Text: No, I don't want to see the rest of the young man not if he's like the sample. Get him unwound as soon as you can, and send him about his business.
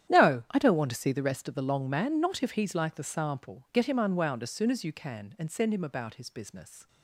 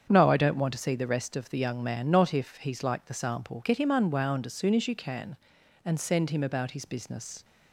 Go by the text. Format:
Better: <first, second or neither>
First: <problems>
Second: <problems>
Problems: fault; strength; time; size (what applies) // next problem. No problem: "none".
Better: second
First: starts louder than the rest; strong; until 1.1 s; 10 dB // says "long" for "young"; at 1.6 s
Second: starts louder than the rest; strong; until 1.1 s; 7.5 dB